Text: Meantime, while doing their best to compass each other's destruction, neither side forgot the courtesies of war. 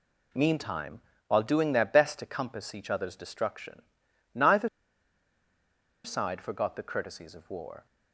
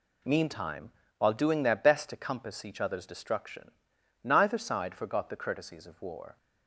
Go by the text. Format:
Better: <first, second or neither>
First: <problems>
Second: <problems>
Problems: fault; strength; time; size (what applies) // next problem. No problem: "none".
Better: second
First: pauses between "neither" and "side"; strong; at 4.6 s; 1.3 s long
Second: none